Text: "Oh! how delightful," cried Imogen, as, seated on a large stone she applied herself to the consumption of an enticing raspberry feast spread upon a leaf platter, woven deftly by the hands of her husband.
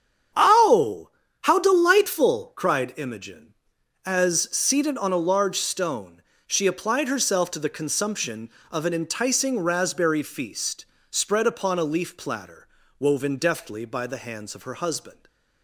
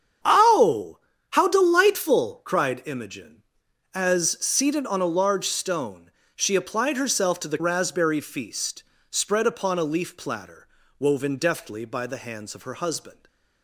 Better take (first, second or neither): first